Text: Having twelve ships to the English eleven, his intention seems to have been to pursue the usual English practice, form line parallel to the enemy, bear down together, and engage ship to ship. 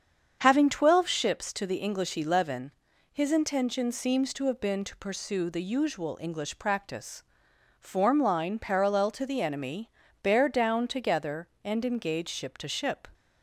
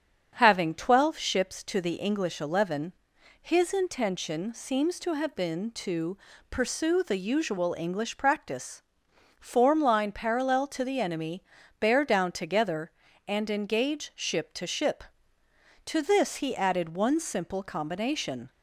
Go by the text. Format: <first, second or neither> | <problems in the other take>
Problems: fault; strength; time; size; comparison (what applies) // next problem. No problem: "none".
first | starts louder than the rest; strong; until 1.3 s; 7.5 dB; strong in the first // pauses between "to" and "pursue"; slight; at 6.1 s; 0.32 s long // goes on to say "To this he added one simple combination"; strong; from 15.8 s on; 2.6 s long